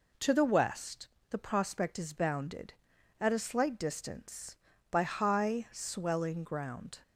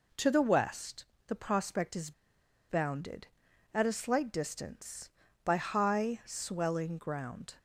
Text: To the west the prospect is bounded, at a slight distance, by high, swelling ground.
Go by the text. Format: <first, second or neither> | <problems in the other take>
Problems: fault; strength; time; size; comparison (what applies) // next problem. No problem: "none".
first | pauses between "west" and "the"; slight; at 1.0 s; 0.22 s long; slight in the first // pauses between "is" and "bounded"; noticeable; at 2.1 s; 0.58 s long